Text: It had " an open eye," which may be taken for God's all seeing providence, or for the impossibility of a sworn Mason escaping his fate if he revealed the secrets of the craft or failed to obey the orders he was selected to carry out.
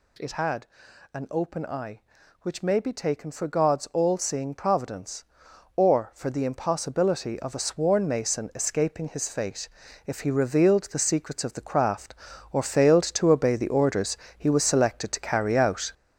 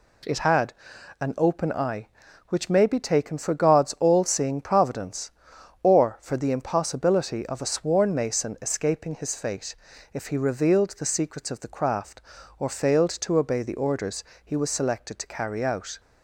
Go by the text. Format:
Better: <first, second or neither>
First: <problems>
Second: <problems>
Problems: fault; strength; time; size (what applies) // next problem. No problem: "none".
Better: second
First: gets louder; strong; throughout; 7.5 dB // pauses between "fate" and "if"; at 9.6 s; 0.38 s long // pauses between "orders" and "he"; slight; at 14.1 s; 0.18 s long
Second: pauses between "fate" and "if"; at 9.7 s; 0.38 s long // pauses between "orders" and "he"; slight; at 14.2 s; 0.18 s long